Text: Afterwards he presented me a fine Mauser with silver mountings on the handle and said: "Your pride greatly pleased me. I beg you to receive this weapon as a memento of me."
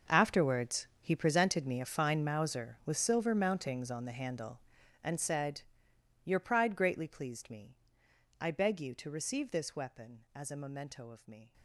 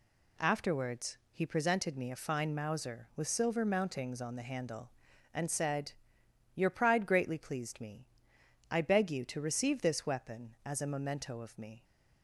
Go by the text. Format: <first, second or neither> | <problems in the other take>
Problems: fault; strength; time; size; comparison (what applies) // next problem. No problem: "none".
second | gets quieter; strong; throughout; 16.5 dB